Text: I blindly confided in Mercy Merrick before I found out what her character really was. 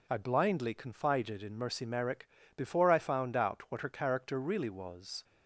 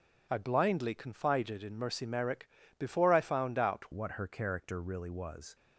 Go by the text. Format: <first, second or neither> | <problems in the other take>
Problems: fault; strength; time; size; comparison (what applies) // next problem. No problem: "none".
first | pauses between "Merrick" and "before"; slight; at 2.4 s; 0.30 s long; slight in the first // changes voice at "what"; from 3.9 s on; 1.6 s long